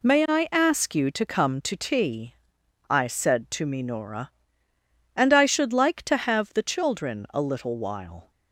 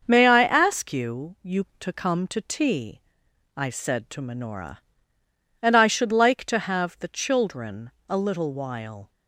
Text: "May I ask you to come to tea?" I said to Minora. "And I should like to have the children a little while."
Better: first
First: none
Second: starts louder than the rest; until 1.0 s; 6.5 dB // says "you" twice; at 1.4 s // pauses between "children" and "a"; slight; at 7.9 s; 0.16 s long

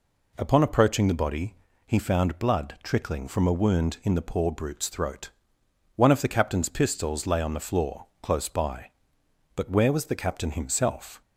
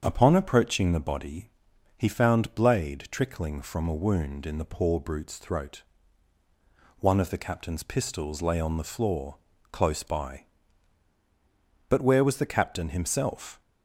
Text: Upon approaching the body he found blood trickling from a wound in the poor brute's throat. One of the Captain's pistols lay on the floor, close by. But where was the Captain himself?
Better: first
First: pauses between "body" and "he"; slight; at 1.5 s; 0.32 s long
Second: starts louder than the rest; strong; until 1.0 s; 7.5 dB // pauses between "body" and "he"; noticeable; at 1.4 s; 0.48 s long // says "blade" for "blood"; at 2.5 s

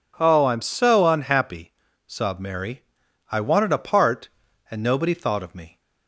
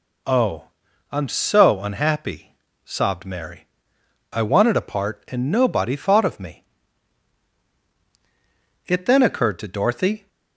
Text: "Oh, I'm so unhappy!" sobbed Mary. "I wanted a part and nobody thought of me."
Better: first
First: none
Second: goes on to say "It then occurred to Dorothy"; from 8.8 s on; 1.4 s long

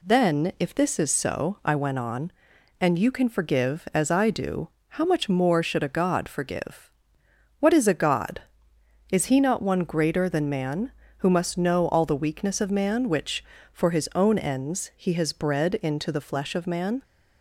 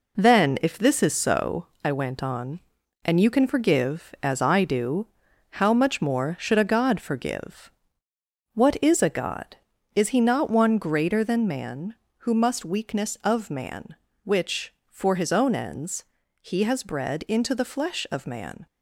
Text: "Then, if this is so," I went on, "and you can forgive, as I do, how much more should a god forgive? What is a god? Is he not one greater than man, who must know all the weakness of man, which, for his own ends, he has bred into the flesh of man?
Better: first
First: none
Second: skips "know all the"; at 12.6 s

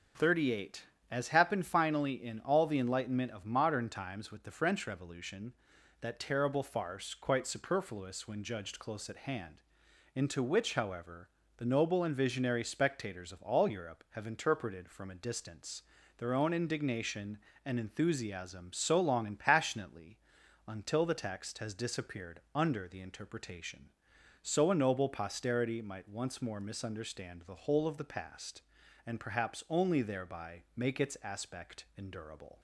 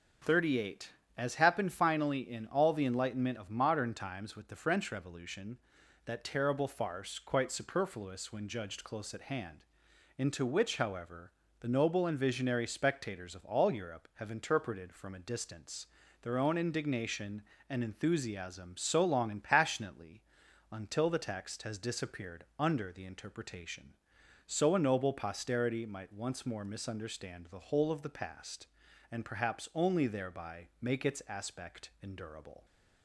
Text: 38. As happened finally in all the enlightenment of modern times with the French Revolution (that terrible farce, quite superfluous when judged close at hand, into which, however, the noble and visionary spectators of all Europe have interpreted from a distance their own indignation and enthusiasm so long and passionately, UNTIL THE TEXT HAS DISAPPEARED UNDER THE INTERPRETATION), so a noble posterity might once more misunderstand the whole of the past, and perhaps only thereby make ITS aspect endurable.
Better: neither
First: starts louder than the rest; until 1.4 s; 6.5 dB // pauses between "distance" and "their"; slight; at 15.8 s; 0.36 s long // pauses between "DISAPPEARED" and "UNDER"; slight; at 22.3 s; 0.16 s long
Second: starts louder than the rest; until 1.5 s; 6.5 dB // pauses between "distance" and "their"; slight; at 15.8 s; 0.36 s long // pauses between "DISAPPEARED" and "UNDER"; slight; at 22.4 s; 0.16 s long

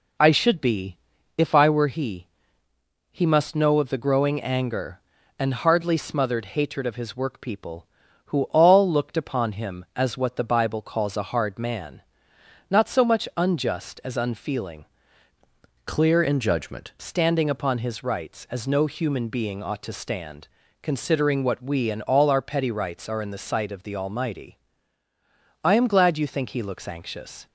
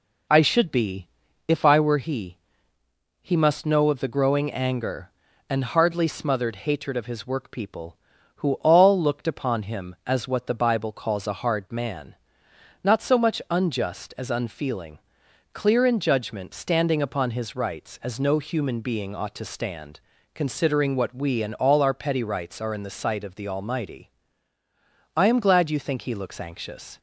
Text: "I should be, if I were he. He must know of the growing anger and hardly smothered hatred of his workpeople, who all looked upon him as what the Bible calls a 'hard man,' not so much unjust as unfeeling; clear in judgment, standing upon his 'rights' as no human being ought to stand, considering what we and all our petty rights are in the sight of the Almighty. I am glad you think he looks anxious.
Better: second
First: changes voice from "clear" to "judgment"; from 15.8 to 16.9 s; 1.1 s long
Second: none

